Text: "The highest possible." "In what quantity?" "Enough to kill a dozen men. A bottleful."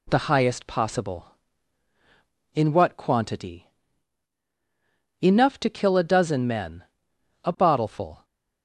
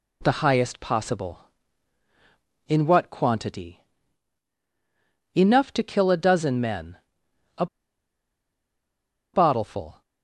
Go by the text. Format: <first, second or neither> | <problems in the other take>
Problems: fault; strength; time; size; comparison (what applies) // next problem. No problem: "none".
first | pauses between "A" and "bottleful"; strong; at 7.6 s; 1.6 s long